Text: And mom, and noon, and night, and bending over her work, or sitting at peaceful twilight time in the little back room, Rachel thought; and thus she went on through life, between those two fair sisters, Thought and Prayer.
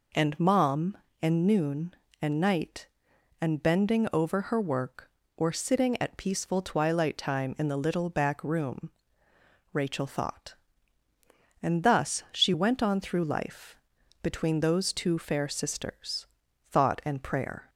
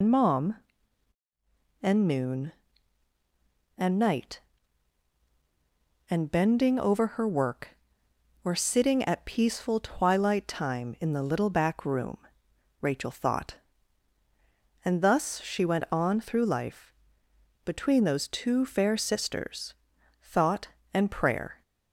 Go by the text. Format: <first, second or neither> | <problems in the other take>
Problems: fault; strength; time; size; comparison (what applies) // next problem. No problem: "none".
first | loses the start of "And"; at 0.0 s; 90 ms